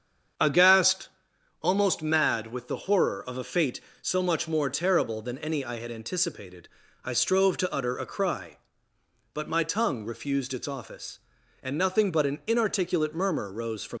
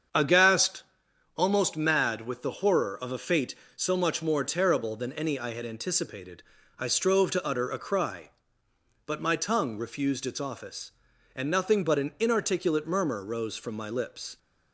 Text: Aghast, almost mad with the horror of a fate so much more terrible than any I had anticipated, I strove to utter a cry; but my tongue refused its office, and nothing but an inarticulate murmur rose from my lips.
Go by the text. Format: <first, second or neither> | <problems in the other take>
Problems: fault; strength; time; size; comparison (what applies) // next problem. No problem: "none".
second | starts louder than the rest; strong; until 1.9 s; 7.5 dB; strong in the second // stops before "my lips"; at 13.9 s